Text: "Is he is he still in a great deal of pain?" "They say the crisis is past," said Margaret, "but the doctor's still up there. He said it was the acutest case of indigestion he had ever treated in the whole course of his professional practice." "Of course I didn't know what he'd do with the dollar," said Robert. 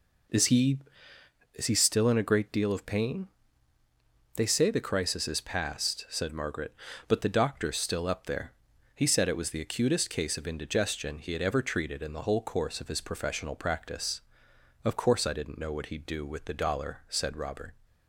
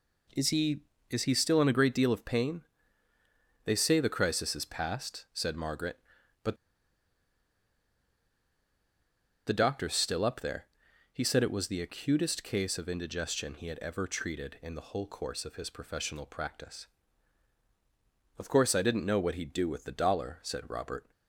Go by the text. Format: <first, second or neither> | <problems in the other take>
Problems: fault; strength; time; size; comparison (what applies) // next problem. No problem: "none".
first | pauses between "but" and "the"; strong; at 6.5 s; 2.8 s long